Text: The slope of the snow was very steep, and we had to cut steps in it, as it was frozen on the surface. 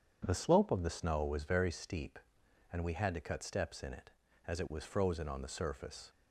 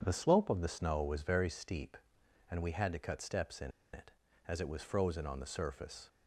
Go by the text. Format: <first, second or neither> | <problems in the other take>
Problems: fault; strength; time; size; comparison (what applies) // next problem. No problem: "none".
first | pauses between "in" and "it"; slight; at 3.6 s; 0.23 s long